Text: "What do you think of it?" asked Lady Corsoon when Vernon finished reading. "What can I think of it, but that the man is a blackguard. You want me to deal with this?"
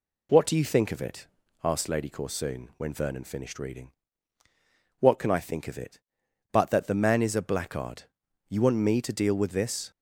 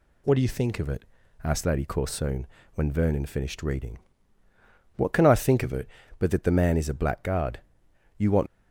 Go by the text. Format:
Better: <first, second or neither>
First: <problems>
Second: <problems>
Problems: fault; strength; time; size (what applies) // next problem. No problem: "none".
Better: first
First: none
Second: pauses between "Corsoon" and "when"; slight; at 2.4 s; 0.26 s long // stops before "me to deal with this"; at 8.4 s